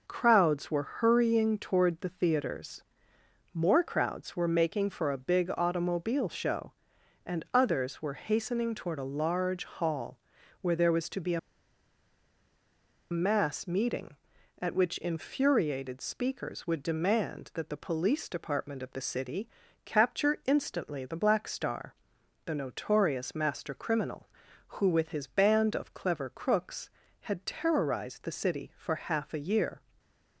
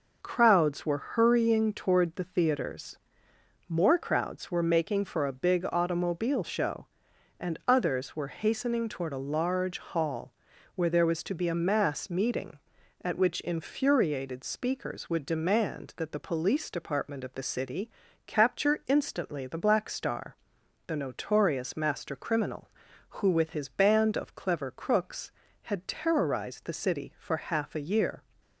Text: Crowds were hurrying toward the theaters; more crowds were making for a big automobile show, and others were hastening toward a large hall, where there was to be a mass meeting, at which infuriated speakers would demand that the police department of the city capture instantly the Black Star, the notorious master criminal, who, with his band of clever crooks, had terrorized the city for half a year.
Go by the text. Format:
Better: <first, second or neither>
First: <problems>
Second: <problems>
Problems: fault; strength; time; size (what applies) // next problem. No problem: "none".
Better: second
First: pauses between "a" and "mass"; strong; at 11.3 s; 1.7 s long // pauses between "city" and "capture"; at 19.4 s; 0.38 s long // stays silent after the last word; slight; from 29.7 s on; 0.6 s long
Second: pauses between "city" and "capture"; at 17.8 s; 0.38 s long